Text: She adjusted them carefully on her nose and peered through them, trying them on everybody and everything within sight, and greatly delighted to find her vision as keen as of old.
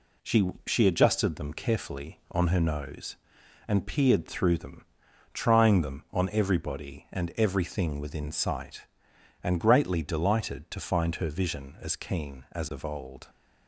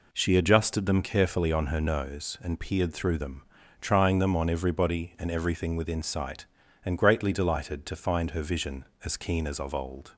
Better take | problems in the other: second | says "She" twice; at 0.6 s

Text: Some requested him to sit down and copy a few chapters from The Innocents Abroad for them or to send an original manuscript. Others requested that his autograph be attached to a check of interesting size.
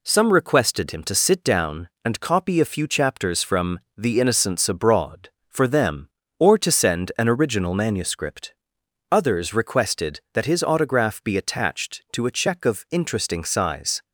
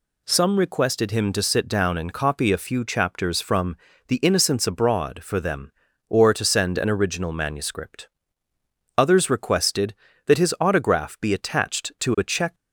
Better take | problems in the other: first | pauses between "from" and "The"; slight; at 3.7 s; 0.30 s long; slight in the first // stops before "of interesting size"; at 12.5 s

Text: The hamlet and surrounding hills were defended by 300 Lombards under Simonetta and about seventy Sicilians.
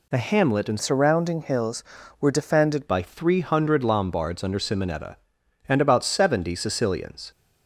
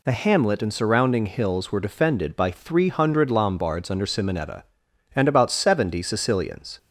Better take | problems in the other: second | changes voice from "surrounding" to "defended"; from 0.8 to 2.8 s; 2.0 s long

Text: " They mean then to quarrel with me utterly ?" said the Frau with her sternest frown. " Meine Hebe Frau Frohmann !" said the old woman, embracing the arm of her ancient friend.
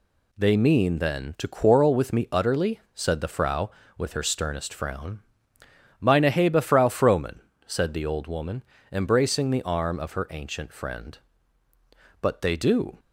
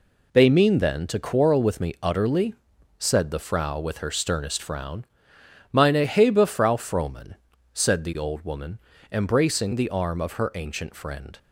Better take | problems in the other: second | goes on to say "But they do"; noticeable; from 12.2 s on; 0.76 s long

